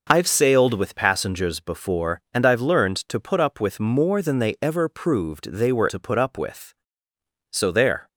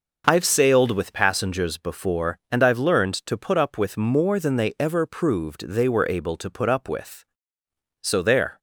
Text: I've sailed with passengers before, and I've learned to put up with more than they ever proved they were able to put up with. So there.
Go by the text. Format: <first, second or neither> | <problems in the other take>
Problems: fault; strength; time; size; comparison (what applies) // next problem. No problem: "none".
second | skips "able"; at 5.8 s